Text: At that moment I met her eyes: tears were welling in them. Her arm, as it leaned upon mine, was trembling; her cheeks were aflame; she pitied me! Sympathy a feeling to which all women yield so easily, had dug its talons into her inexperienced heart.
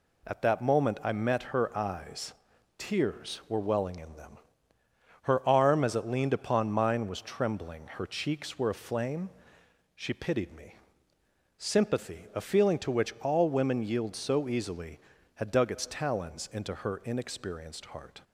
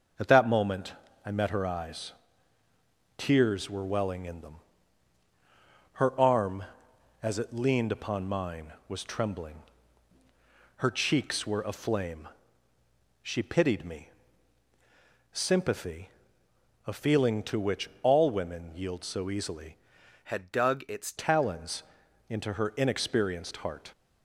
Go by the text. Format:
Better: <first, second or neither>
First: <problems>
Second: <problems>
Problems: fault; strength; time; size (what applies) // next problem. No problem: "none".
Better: first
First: none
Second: pauses between "moment" and "I"; slight; at 0.9 s; 0.32 s long // pauses between "Sympathy" and "a"; noticeable; at 16.1 s; 0.76 s long // changes voice from "had" to "its"; from 20.2 to 21.1 s; 0.9 s long // pauses between "talons" and "into"; noticeable; at 21.8 s; 0.46 s long